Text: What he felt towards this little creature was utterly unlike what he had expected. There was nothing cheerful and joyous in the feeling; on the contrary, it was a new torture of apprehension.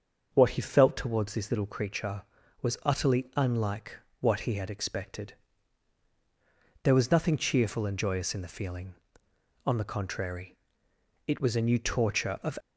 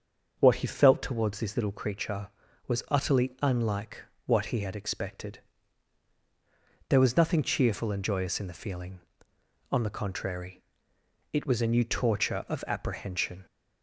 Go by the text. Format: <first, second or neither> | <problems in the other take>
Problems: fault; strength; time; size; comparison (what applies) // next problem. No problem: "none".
second | starts louder than the rest; until 1.3 s; 6.5 dB; also in the second // pauses between "unlike" and "what"; slight; at 3.9 s; 0.24 s long; slight in the second // stops before "apprehension"; at 12.5 s